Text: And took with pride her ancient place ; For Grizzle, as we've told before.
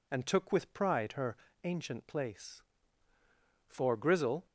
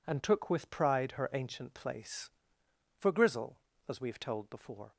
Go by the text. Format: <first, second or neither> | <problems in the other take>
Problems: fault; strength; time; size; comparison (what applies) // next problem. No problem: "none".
second | pauses between "her" and "ancient"; slight; at 1.3 s; 0.30 s long // stops before "as we've told before"; at 4.4 s